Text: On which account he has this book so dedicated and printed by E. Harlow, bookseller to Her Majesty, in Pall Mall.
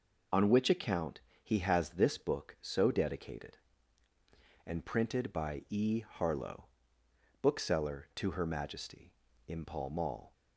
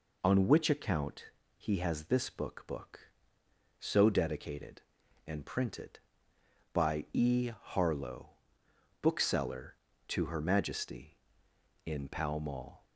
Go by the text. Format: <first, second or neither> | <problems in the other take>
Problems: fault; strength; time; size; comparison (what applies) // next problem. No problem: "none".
first | pauses between "account" and "he"; slight; at 1.2 s; 0.26 s long; slight in the first // says "book" twice; at 2.6 s